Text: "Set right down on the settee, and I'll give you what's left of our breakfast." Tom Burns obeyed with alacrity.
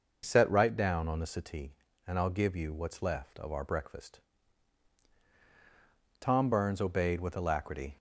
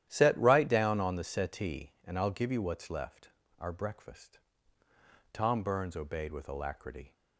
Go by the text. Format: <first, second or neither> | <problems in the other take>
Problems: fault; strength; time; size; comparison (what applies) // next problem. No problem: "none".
first | starts louder than the rest; strong; until 1.1 s; 11.5 dB // skips "of"; at 3.4 s